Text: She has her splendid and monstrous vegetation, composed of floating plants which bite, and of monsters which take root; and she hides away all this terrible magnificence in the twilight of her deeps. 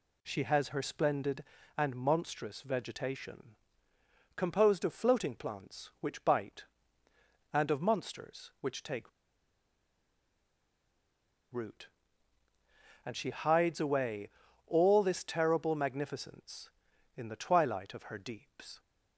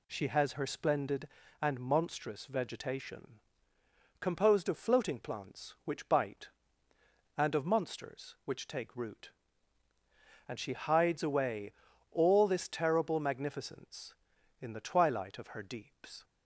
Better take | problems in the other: second | pauses between "take" and "root"; strong; at 9.1 s; 2.4 s long // pauses between "away" and "all"; at 14.2 s; 0.38 s long; also in the second

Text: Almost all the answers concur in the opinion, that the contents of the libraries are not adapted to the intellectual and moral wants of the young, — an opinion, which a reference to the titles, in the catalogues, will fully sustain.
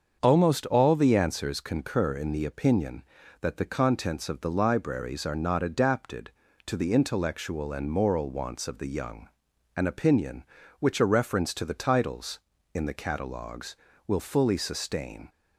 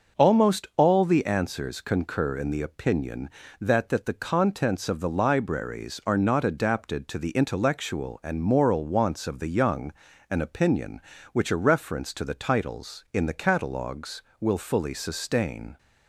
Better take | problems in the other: first | starts louder than the rest; until 1.2 s; 6.5 dB; also in the first // says "that" twice; at 3.8 s

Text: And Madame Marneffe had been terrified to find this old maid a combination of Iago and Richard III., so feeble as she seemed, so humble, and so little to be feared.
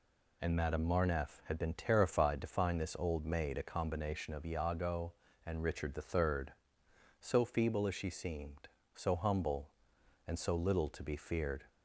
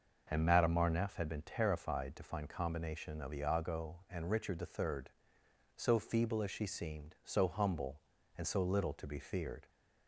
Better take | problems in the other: first | skips "this old maid a"; at 2.4 s

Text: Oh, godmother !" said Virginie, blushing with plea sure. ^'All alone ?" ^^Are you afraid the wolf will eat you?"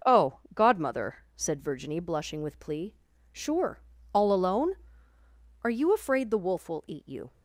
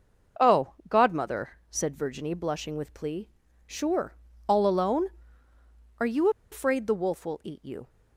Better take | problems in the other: first | starts louder than the rest; until 1.5 s; 6.5 dB; also in the first // pauses between "plea" and "sure"; at 3.2 s; 0.38 s long; also in the first // pauses between "you" and "afraid"; slight; at 6.2 s; 0.22 s long

